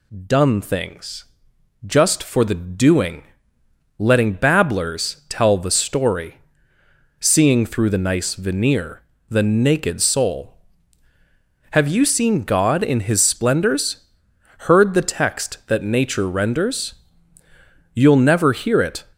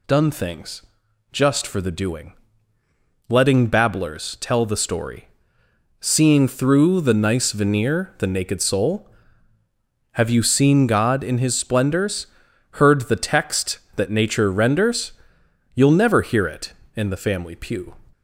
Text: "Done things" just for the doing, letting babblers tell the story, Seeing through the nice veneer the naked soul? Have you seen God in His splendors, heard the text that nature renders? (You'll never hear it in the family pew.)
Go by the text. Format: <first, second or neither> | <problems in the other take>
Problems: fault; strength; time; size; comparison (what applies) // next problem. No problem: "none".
second | pauses between "things" and "just"; noticeable; at 1.2 s; 0.60 s long; noticeable in the second // pauses between "veneer" and "the"; slight; at 9.0 s; 0.26 s long // stops before "in the family pew"; at 19.1 s